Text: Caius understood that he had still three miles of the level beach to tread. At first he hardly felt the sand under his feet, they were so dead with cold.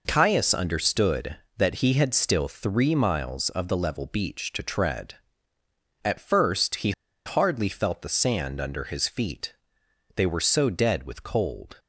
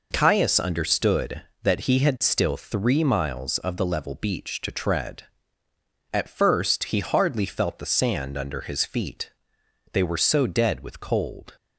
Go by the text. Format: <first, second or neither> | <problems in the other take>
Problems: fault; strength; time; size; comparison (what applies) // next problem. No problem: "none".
second | pauses between "he" and "hardly"; slight; at 6.9 s; 0.33 s long